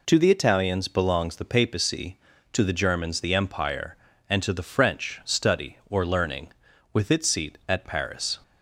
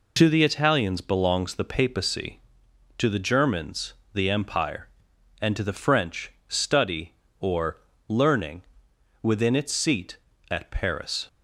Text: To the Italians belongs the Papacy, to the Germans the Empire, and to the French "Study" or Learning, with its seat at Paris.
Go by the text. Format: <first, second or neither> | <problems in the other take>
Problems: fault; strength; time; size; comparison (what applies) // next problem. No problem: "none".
first | pauses between "Germans" and "the"; slight; at 3.9 s; 0.22 s long // pauses between "French" and "Study"; slight; at 6.3 s; 0.16 s long // pauses between "or" and "Learning"; slight; at 7.7 s; 0.30 s long // says "within" for "with"; at 9.2 s